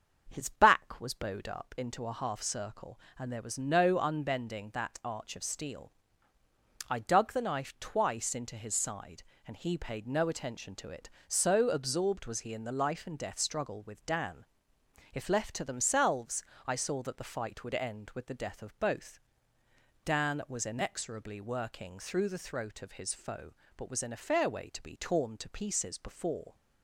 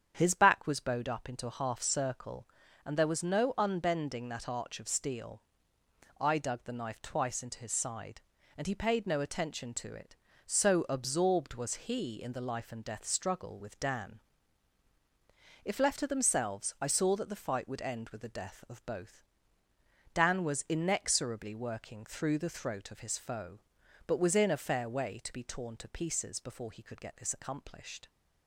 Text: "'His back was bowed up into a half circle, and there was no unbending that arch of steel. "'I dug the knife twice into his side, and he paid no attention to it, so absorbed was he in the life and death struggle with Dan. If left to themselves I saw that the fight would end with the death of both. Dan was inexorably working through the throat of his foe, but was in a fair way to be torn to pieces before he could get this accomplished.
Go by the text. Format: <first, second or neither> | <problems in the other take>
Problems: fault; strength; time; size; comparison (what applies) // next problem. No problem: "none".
second | starts louder than the rest; until 1.3 s; 7 dB; strong in the second // pauses between "themselves" and "I"; slight; at 16.4 s; 0.22 s long // stops before "he could get this accomplished"; at 26.5 s